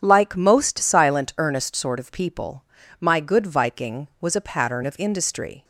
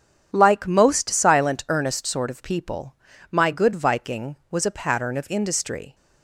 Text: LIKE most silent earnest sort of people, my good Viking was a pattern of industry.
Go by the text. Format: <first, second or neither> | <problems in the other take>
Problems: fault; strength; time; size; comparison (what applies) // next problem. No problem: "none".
neither | starts louder than the rest; strong; the same in both